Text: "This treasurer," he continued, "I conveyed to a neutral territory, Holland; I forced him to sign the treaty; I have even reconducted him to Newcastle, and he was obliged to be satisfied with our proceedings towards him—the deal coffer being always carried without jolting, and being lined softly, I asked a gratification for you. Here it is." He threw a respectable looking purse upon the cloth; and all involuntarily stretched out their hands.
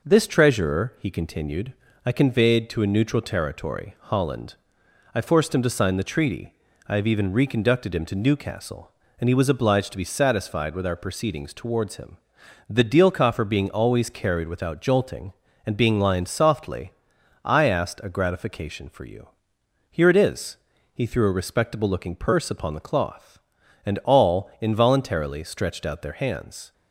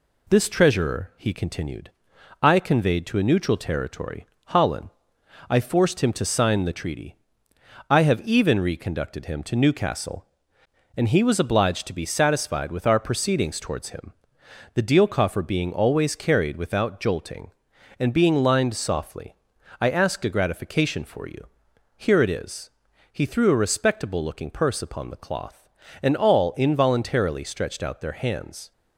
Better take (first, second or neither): neither